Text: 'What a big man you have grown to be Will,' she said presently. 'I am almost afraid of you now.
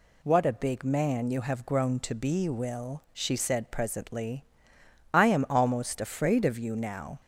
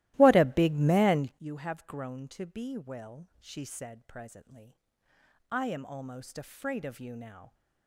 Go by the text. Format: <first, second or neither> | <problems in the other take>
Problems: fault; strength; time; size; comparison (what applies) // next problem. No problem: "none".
first | starts louder than the rest; strong; until 1.3 s; 16.5 dB